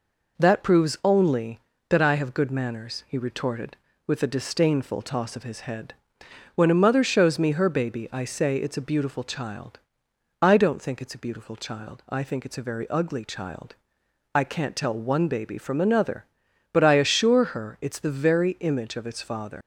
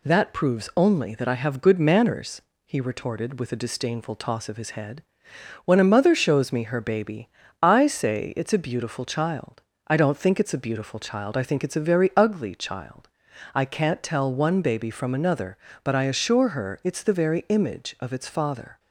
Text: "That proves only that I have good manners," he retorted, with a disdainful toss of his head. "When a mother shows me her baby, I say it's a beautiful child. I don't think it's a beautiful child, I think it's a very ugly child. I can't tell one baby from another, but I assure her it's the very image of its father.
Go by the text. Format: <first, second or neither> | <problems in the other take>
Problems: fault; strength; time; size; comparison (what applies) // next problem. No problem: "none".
second | leaves "father" unfinished; at 19.6 s; 90 ms